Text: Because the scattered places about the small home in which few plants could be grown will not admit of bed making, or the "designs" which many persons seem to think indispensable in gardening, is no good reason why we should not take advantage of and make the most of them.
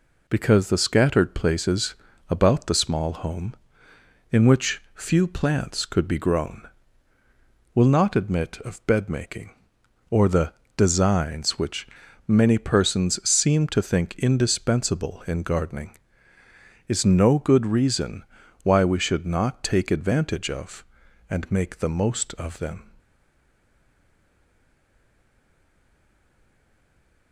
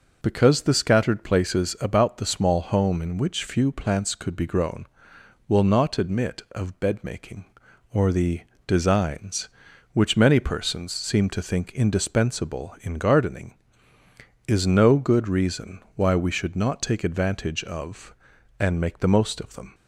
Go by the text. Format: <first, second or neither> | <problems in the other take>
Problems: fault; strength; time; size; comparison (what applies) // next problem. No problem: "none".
second | pauses between "places" and "about"; slight; at 1.9 s; 0.34 s long // pauses between "the" and "designs"; slight; at 10.5 s; 0.22 s long; slight in the second // pauses between "which" and "many"; at 11.8 s; 0.40 s long // pauses between "reason" and "why"; at 18.2 s; 0.40 s long; slight in the second // stays silent after the last word; strong; from 22.9 s on; 4.4 s long